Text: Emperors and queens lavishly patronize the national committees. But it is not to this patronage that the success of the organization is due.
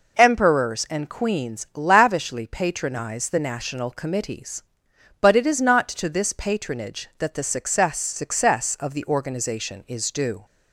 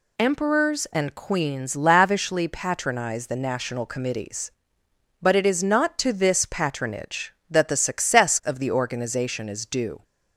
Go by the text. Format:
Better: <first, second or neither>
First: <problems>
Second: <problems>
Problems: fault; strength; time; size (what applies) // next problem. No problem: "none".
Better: second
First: says "success" twice; at 7.9 s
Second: none